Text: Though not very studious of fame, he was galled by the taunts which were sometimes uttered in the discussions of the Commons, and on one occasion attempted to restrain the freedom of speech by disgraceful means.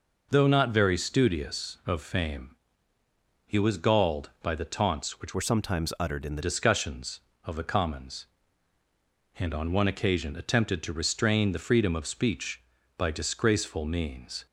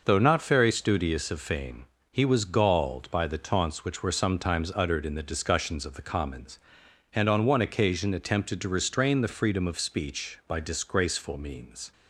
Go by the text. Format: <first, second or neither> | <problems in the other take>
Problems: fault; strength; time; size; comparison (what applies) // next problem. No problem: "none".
second | changes voice from "were" to "the"; from 5.3 to 6.4 s; 1.1 s long